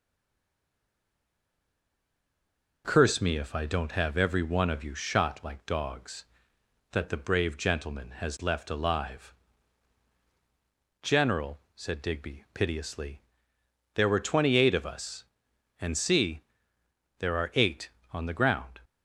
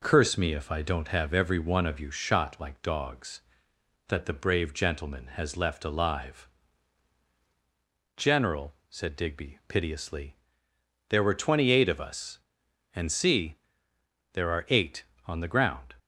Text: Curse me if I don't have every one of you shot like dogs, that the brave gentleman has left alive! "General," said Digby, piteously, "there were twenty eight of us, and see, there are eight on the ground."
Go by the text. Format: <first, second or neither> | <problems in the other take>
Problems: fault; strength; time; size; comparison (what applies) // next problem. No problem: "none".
second | stays silent before the first word; strong; until 2.8 s; 2.8 s long